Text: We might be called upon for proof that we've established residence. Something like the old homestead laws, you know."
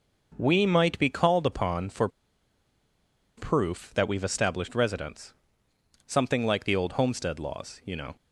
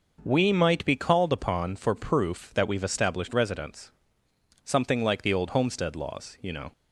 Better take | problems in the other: second | pauses between "for" and "proof"; strong; at 2.0 s; 1.2 s long

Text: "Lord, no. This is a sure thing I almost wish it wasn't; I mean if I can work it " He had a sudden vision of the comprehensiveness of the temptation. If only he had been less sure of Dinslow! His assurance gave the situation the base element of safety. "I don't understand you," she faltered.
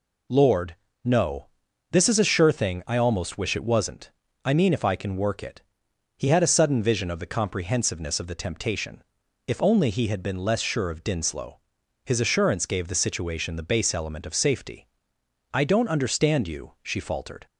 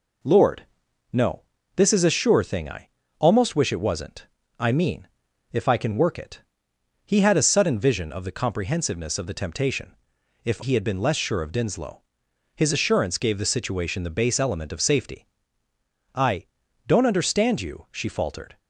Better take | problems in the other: first | pauses between "I" and "almost"; slight; at 2.8 s; 0.30 s long // pauses between "mean" and "if"; noticeable; at 5.0 s; 0.46 s long // skips "only"; at 10.6 s // pauses between "I" and "don't"; at 16.4 s; 0.40 s long

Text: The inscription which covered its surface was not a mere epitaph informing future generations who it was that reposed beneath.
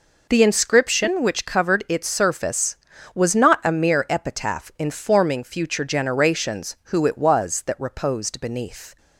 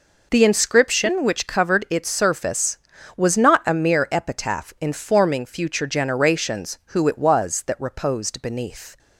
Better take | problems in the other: neither | none

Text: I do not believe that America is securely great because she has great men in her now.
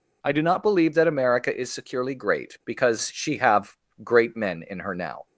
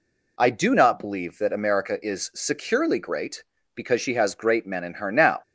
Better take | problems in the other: second | says "have" for "has"; at 3.3 s

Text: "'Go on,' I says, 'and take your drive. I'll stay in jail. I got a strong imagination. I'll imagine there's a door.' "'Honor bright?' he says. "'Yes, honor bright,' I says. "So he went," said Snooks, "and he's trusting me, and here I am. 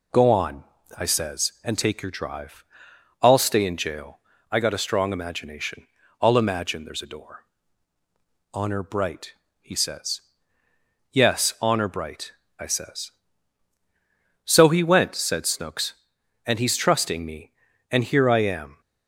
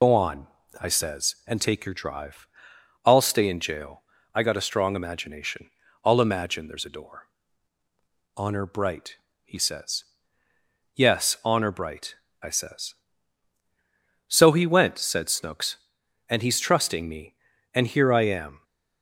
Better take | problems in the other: first | loses the start of "Go"; at 0.0 s; 65 ms

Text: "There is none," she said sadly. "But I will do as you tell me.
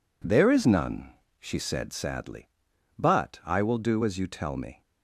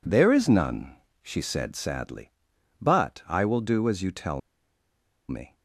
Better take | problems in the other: first | pauses between "tell" and "me"; noticeable; at 4.4 s; 0.90 s long

